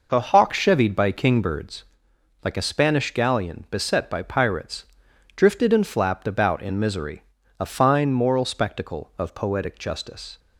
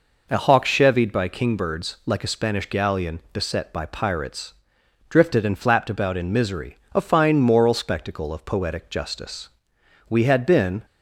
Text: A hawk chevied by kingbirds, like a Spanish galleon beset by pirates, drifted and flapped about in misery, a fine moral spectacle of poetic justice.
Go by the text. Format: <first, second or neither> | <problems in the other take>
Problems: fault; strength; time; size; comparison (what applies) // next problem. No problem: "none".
first | goes on to say "We had been"; noticeable; from 10.0 s on; 0.76 s long